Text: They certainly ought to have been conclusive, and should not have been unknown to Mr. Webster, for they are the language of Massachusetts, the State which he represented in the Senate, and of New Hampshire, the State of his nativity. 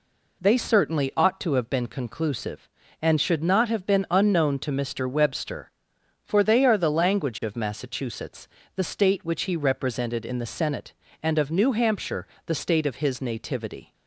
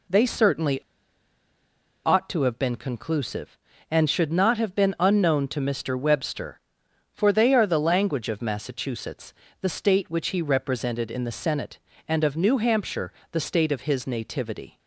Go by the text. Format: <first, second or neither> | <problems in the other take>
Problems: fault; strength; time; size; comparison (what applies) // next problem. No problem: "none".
first | pauses between "certainly" and "ought"; strong; at 0.7 s; 1.2 s long